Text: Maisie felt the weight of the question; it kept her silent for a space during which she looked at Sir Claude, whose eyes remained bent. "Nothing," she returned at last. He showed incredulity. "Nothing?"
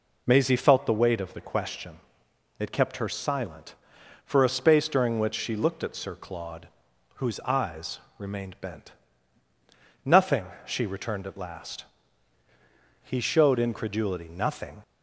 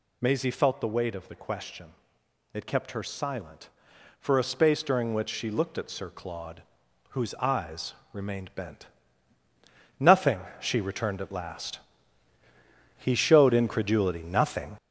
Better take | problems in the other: first | gets louder; noticeable; throughout; 5.5 dB // pauses between "eyes" and "remained"; slight; at 7.9 s; 0.18 s long; slight in the first

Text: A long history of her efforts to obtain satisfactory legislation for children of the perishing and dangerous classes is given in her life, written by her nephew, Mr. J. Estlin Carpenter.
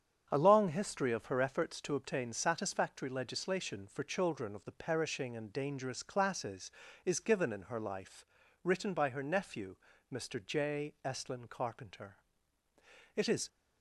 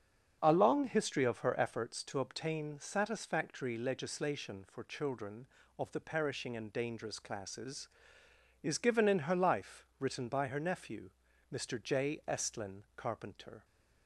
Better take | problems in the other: second | starts louder than the rest; strong; until 1.3 s; 7.5 dB; also in the second // goes on to say "It is"; slight; from 13.1 s on; 0.32 s long

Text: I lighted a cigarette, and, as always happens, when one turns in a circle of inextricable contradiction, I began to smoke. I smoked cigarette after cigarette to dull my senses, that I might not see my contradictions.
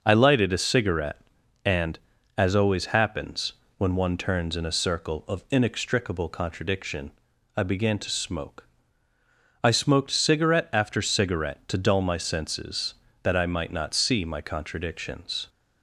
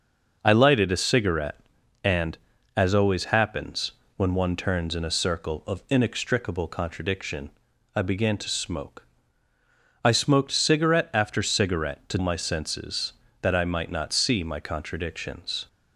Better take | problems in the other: first | skips "dull"; at 12.1 s

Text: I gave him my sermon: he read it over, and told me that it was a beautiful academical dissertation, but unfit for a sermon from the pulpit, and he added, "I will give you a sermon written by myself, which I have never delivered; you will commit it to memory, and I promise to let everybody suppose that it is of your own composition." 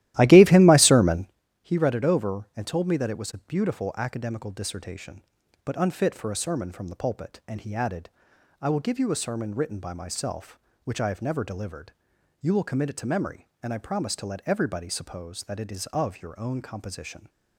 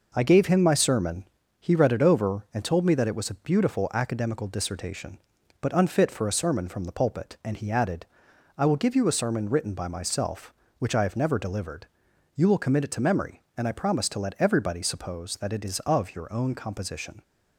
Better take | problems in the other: second | starts louder than the rest; strong; until 1.3 s; 14.5 dB

